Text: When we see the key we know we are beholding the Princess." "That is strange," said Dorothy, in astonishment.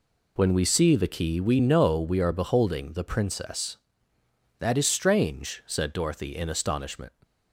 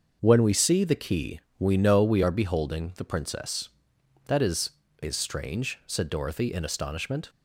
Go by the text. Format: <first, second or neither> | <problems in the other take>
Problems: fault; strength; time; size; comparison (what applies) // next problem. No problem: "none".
first | starts louder than the rest; until 1.2 s; 6.5 dB // pauses between "key" and "we"; slight; at 1.3 s; 0.18 s long // says "is" twice; at 4.9 s